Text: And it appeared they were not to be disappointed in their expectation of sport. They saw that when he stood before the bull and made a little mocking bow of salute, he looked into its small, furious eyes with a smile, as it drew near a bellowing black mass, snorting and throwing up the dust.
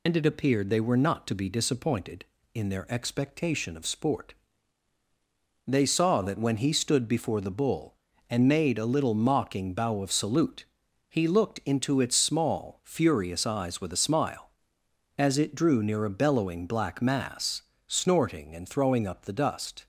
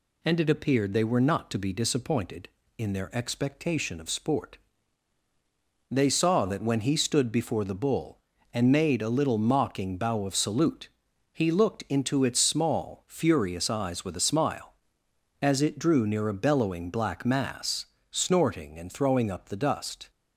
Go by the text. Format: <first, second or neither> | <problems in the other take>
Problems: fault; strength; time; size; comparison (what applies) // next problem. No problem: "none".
second | loses the start of "And"; at 0.0 s; 55 ms